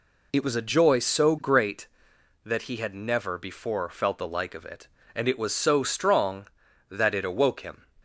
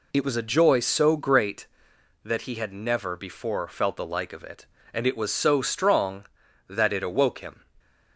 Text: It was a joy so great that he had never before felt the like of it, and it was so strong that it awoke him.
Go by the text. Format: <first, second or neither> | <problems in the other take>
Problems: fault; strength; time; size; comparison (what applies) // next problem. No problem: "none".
neither | none